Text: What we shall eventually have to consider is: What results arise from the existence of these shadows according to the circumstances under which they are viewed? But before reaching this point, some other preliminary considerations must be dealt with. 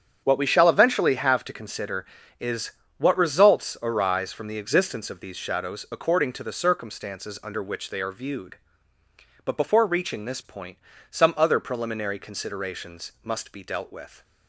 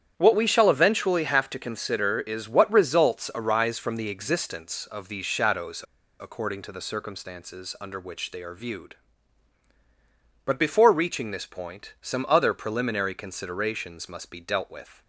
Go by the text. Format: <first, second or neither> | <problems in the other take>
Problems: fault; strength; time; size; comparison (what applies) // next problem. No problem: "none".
first | starts louder than the rest; strong; until 1.1 s; 9.5 dB; strong in the first // pauses between "shadows" and "according"; at 5.8 s; 0.38 s long